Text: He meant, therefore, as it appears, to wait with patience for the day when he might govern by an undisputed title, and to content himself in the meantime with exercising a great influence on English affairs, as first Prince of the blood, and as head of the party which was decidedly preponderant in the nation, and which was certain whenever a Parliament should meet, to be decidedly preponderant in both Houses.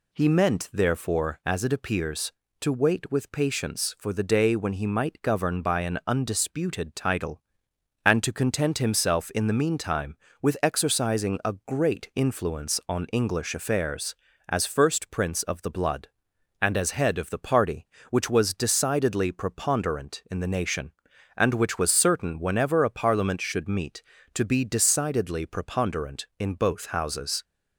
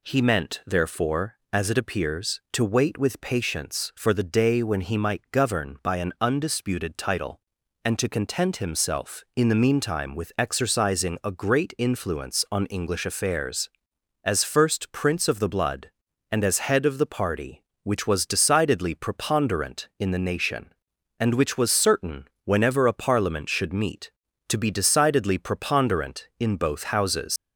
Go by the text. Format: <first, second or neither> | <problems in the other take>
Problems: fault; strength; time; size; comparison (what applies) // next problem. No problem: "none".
first | pauses between "certain" and "whenever"; slight; at 22.2 s; 0.16 s long // leaves "Houses" unfinished; at 27.3 s; 120 ms